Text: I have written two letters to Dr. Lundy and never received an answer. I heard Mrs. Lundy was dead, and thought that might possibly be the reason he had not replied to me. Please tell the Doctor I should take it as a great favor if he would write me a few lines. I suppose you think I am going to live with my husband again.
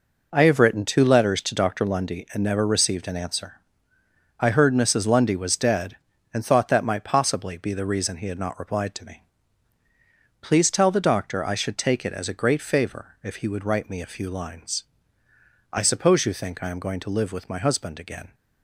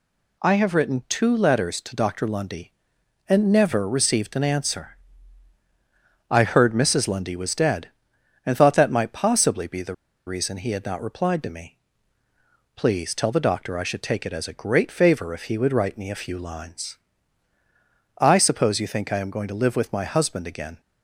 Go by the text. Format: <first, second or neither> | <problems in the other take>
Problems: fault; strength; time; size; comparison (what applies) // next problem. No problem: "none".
first | pauses between "the" and "reason"; slight; at 9.9 s; 0.32 s long